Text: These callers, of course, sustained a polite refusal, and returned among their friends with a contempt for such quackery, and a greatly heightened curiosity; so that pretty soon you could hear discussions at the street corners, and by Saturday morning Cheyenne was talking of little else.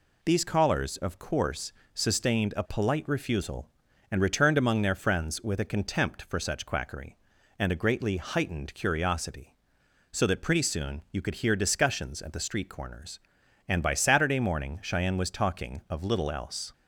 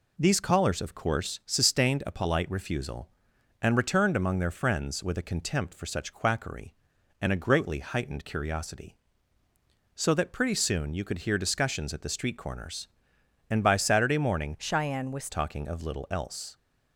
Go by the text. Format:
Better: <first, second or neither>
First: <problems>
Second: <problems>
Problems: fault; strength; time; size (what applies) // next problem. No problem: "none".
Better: first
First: none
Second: changes voice from "Cheyenne" to "was"; from 14.5 to 15.3 s; 0.8 s long